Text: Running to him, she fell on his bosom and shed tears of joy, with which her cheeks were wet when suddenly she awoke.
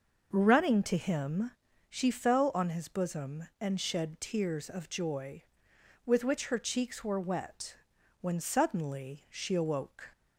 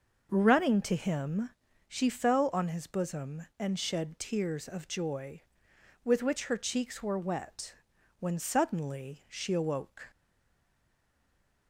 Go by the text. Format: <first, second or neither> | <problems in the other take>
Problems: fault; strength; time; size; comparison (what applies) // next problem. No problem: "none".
first | starts louder than the rest; noticeable; until 1.3 s; 6 dB; noticeable in the first // pauses between "wet" and "when"; noticeable; at 7.7 s; 0.46 s long; noticeable in the first // stays silent after the last word; noticeable; from 10.1 s on; 1.5 s long